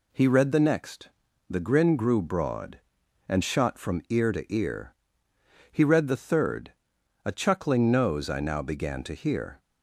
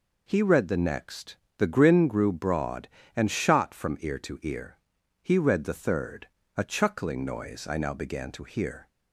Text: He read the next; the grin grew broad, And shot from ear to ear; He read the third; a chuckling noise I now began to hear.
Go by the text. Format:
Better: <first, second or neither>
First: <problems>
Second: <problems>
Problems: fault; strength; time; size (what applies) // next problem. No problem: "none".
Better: second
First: says "nose" for "noise"; at 7.9 s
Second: none